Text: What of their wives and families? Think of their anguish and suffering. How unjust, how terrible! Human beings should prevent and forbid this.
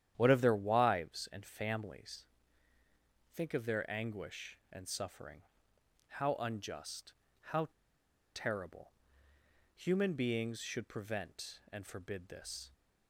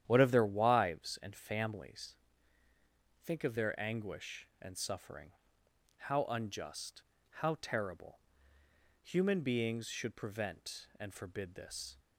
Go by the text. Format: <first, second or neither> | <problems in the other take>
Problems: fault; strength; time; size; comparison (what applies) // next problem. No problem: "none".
second | starts louder than the rest; strong; until 1.1 s; 10.5 dB; strong in the second // pauses between "how" and "terrible"; noticeable; at 7.6 s; 0.68 s long